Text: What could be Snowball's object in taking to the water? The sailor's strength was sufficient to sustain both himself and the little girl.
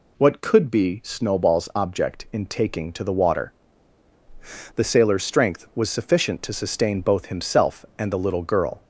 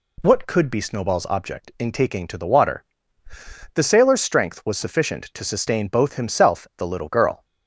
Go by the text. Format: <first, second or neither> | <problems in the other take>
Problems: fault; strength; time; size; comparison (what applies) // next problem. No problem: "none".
first | skips "and"; at 6.7 s